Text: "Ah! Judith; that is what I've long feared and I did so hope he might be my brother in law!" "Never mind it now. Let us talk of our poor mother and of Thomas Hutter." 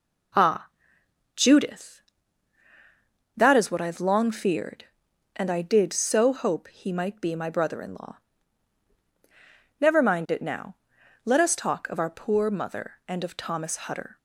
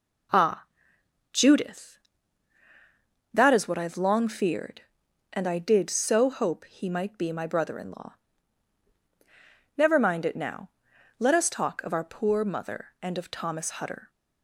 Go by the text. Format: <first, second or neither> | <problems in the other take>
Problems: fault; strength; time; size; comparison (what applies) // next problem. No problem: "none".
neither | none